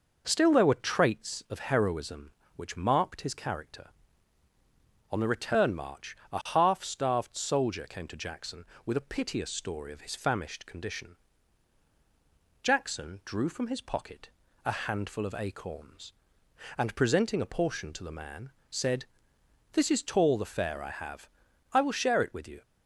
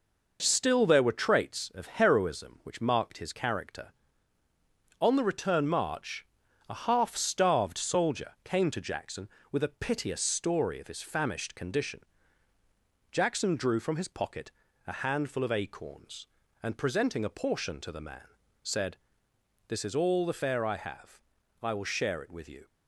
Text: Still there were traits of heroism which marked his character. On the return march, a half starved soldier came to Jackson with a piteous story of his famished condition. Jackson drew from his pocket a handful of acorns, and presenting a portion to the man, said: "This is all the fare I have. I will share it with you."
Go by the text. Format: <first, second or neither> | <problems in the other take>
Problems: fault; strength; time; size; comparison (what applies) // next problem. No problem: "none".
second | pauses between "pocket" and "a"; slight; at 14.2 s; 0.34 s long; slight in the second // says "tall" for "all"; at 20.0 s